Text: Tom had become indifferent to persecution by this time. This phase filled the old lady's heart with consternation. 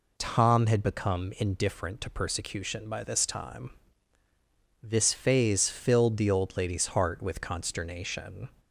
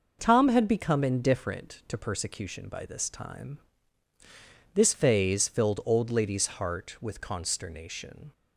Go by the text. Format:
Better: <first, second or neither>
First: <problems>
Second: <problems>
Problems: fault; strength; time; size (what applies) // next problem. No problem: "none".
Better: first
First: none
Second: skips "the"; at 5.8 s